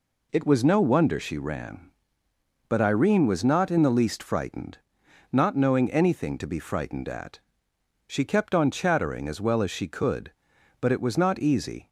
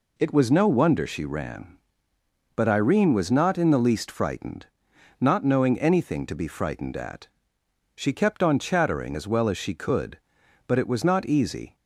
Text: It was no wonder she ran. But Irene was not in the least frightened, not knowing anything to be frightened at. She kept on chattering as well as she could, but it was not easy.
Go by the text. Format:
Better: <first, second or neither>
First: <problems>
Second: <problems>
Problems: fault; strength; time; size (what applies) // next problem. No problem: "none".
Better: neither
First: none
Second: none